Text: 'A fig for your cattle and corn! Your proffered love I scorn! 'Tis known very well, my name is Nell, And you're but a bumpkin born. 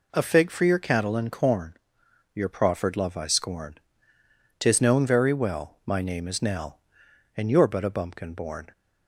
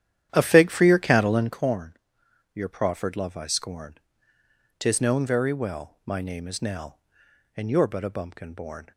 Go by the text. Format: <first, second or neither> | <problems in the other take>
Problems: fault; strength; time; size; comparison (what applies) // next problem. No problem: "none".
first | starts louder than the rest; strong; until 1.6 s; 10.5 dB